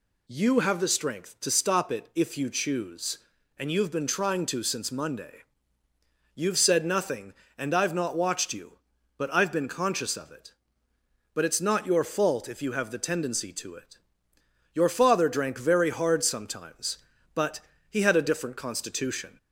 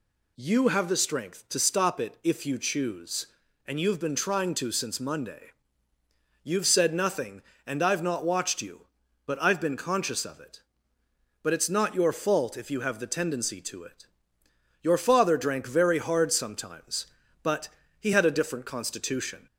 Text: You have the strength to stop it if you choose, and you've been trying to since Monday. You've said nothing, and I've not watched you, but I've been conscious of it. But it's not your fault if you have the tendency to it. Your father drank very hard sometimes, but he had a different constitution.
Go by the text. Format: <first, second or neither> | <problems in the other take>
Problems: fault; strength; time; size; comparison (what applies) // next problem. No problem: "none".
neither | pauses between "but" and "he"; slight; the same in both